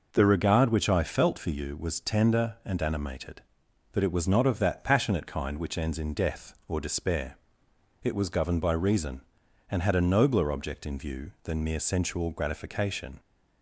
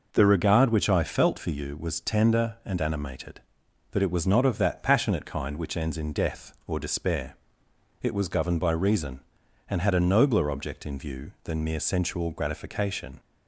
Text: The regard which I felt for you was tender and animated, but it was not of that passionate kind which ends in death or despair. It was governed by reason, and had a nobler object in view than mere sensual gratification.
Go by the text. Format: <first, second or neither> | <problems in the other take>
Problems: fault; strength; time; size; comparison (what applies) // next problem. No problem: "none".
neither | none